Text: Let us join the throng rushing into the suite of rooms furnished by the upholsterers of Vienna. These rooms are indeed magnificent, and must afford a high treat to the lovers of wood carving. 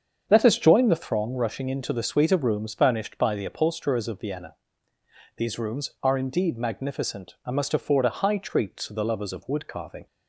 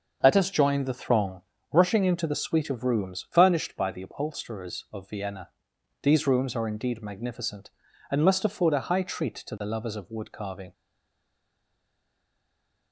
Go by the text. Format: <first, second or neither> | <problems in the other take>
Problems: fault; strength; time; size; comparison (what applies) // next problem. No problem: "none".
first | starts louder than the rest; until 1.2 s; 6.5 dB; strong in the first // pauses between "throng" and "rushing"; slight; at 1.4 s; 0.32 s long // stays silent after the last word; from 10.7 s on; 2.2 s long